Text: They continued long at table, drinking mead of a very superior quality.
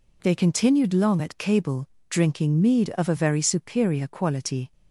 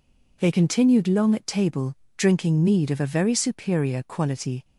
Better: second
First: says "cable" for "table"; at 1.3 s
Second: none

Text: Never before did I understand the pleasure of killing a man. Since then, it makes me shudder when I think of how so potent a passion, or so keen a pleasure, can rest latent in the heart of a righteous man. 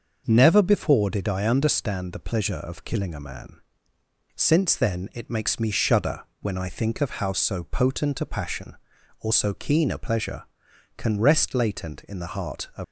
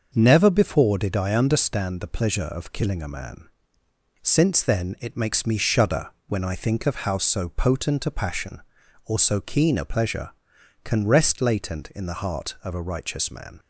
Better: second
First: starts louder than the rest; until 1.2 s; 6 dB // pauses between "shudder" and "when"; slight; at 6.2 s; 0.18 s long // stops before "a righteous man"; at 12.8 s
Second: starts louder than the rest; until 1.1 s; 6 dB // pauses between "shudder" and "when"; slight; at 6.0 s; 0.18 s long

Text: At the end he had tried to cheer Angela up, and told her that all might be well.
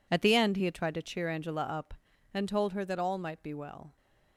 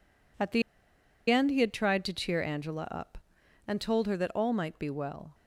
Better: first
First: none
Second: pauses between "the" and "end"; noticeable; at 0.6 s; 0.68 s long

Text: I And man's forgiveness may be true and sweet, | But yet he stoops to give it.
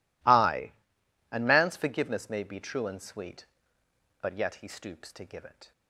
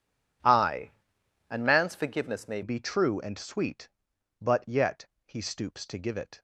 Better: first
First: none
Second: changes voice at "be"; from 2.6 s on; 3.8 s long // pauses between "yet" and "he"; slight; at 5.0 s; 0.18 s long

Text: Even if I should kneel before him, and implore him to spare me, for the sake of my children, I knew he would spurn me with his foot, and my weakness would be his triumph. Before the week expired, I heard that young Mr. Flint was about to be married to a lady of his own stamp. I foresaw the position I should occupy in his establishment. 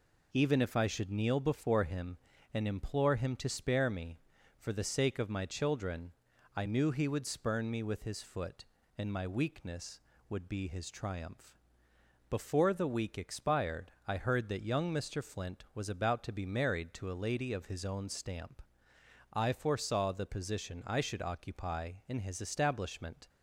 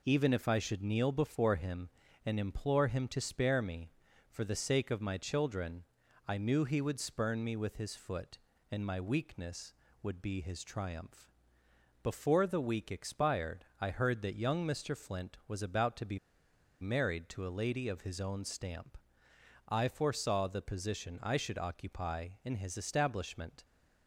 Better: first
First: none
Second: pauses between "be" and "married"; noticeable; at 16.1 s; 0.62 s long

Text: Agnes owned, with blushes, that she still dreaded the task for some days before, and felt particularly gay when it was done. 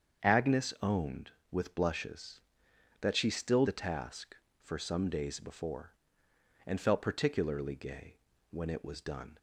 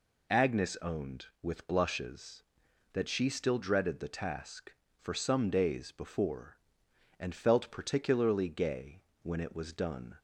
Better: second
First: starts louder than the rest; strong; until 1.3 s; 7.5 dB // skips "dreaded"; at 3.6 s // pauses between "gay" and "when"; slight; at 8.1 s; 0.34 s long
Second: pauses between "gay" and "when"; slight; at 9.0 s; 0.20 s long

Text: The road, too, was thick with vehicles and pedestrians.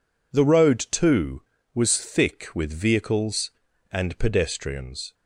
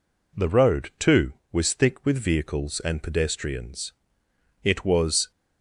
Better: first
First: none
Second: goes on to say "It was"; noticeable; from 4.6 s on; 0.68 s long

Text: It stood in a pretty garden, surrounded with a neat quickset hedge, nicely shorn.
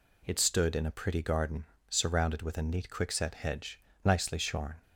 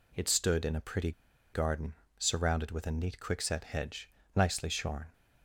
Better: first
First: none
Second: pauses between "pretty" and "garden"; at 1.1 s; 0.42 s long

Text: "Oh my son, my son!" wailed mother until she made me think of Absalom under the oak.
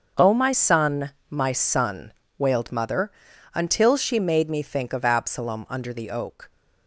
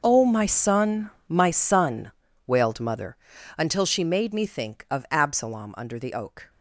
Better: first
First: starts louder than the rest; until 1.3 s; 6.5 dB // pauses between "mother" and "until"; at 3.1 s; 0.42 s long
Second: gets quieter; strong; throughout; 16 dB // starts louder than the rest; noticeable; until 1.0 s; 6 dB // pauses between "mother" and "until"; at 3.1 s; 0.40 s long

